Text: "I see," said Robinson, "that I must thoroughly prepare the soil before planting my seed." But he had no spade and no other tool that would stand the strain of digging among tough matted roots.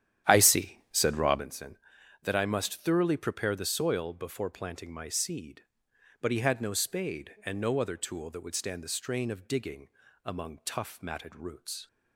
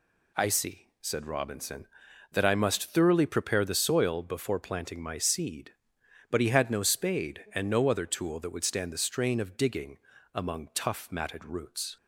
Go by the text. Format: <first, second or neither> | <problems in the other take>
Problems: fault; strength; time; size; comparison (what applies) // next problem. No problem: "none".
second | starts louder than the rest; strong; until 1.5 s; 10.5 dB // pauses between "digging" and "among"; slight; at 9.8 s; 0.34 s long; slight in the second